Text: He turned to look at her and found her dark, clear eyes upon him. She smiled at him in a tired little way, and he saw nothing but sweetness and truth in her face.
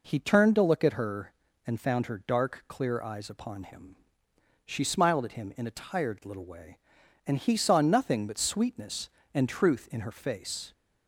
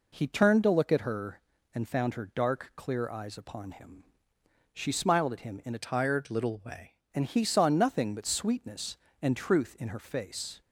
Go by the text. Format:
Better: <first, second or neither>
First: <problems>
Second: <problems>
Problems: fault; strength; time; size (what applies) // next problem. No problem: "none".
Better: first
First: none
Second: changes voice from "tired" to "way"; from 5.7 to 6.9 s; 1.2 s long